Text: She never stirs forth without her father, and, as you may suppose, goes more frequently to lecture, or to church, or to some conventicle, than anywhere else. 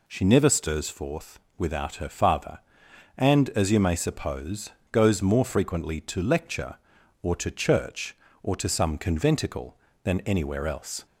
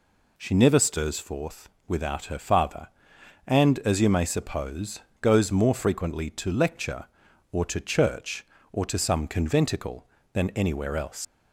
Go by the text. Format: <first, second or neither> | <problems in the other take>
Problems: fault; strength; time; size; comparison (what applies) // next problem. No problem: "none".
first | pauses between "forth" and "without"; slight; at 1.6 s; 0.18 s long; slight in the first // leaves "else" unfinished; at 11.2 s; 95 ms